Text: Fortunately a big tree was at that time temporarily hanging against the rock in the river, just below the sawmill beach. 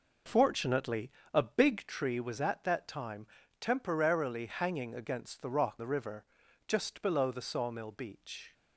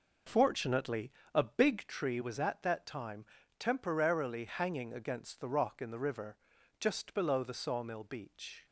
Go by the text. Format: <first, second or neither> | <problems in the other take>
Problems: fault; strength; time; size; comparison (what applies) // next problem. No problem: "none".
second | pauses between "Fortunately" and "a"; slight; at 1.0 s; 0.24 s long; slight in the second // pauses between "time" and "temporarily"; slight; at 3.2 s; 0.34 s long; slight in the second // skips "in"; at 5.7 s